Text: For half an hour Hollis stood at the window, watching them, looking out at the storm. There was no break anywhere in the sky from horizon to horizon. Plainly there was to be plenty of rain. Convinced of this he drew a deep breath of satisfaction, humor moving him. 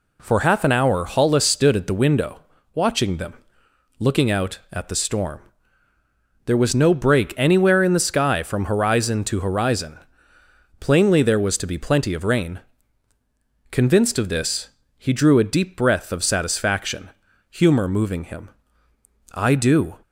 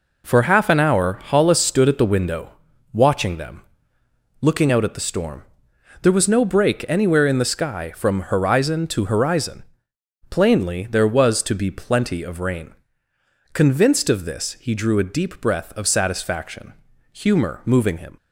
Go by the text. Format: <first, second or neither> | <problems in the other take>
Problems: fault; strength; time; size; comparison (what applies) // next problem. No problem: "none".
second | pauses between "this" and "he"; slight; at 14.6 s; 0.28 s long // goes on to say "I do"; noticeable; from 19.3 s on; 0.64 s long